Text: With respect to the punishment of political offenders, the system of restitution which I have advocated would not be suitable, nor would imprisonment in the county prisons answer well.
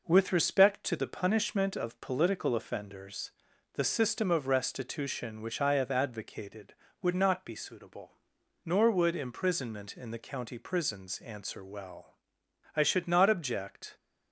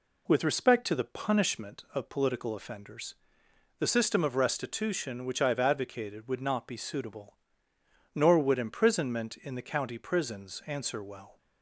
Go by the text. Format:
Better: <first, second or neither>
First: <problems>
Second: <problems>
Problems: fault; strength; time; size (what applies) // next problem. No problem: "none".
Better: second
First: goes on to say "I should not object"; noticeable; from 12.7 s on; 1.2 s long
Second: none